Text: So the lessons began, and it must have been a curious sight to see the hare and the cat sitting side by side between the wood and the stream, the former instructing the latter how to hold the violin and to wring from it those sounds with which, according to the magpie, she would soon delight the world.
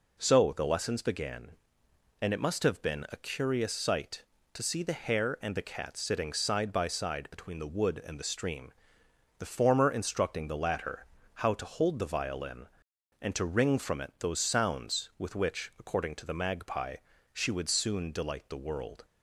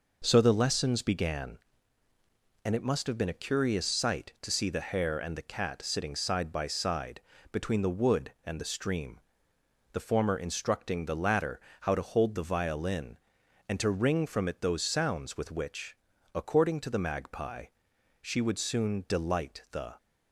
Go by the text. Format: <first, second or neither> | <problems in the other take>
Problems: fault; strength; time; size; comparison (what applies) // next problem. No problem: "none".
first | pauses between "side" and "between"; slight; at 7.1 s; 0.32 s long // pauses between "latter" and "how"; slight; at 11.5 s; 0.22 s long; slight in the first // stops before "world"; at 19.9 s